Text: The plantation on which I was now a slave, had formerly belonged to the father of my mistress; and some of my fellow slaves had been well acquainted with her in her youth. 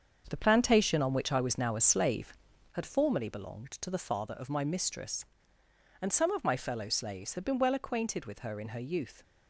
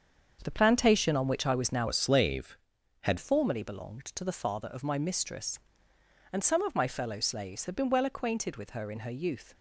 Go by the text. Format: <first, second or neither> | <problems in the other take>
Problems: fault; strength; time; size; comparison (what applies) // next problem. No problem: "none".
first | starts louder than the rest; until 1.4 s; 7 dB; also in the first // changes voice from "a" to "had"; from 1.8 to 3.1 s; 1.3 s long